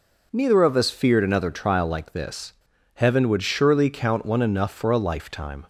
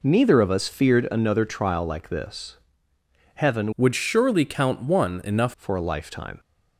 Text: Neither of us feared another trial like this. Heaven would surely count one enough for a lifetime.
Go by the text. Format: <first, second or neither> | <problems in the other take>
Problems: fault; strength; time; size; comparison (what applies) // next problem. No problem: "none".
first | changes voice from "would" to "enough"; from 3.7 to 5.5 s; 1.8 s long